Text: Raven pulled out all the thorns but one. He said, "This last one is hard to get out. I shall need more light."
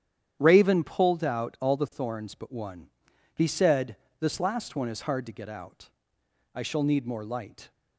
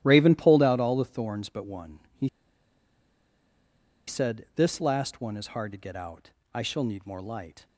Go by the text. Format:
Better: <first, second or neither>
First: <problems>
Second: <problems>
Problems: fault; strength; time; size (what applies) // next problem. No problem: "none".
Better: first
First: starts louder than the rest; strong; until 1.4 s; 9.5 dB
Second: starts louder than the rest; strong; until 1.0 s; 14.5 dB // pauses between "He" and "said"; strong; at 2.2 s; 1.7 s long